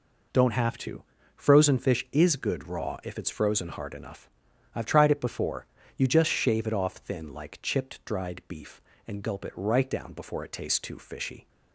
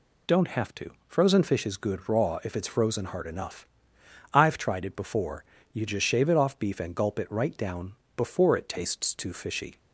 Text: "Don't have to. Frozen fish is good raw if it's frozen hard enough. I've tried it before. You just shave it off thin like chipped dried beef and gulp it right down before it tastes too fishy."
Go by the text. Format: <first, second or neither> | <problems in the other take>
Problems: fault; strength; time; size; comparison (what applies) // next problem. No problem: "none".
first | skips "thin like chipped dried"; at 6.5 s // pauses between "down" and "before"; slight; at 7.9 s; 0.22 s long